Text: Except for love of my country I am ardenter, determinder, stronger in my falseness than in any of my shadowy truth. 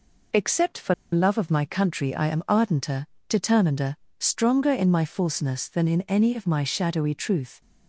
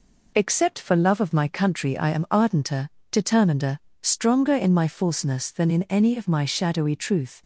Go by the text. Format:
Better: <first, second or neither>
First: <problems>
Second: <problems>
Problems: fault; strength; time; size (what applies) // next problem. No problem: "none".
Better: second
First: pauses between "for" and "love"; slight; at 0.9 s; 0.18 s long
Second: none